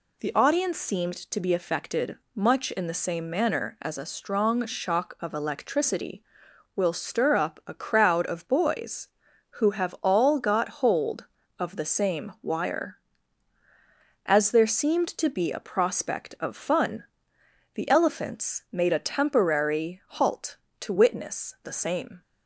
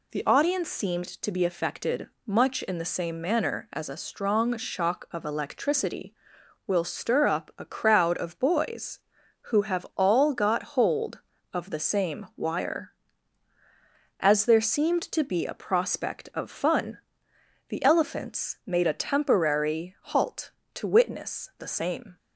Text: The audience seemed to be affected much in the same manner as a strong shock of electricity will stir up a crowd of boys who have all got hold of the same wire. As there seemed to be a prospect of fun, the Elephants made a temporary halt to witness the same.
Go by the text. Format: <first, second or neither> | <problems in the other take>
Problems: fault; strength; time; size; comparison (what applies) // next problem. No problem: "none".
neither | pauses between "affected" and "much"; slight; the same in both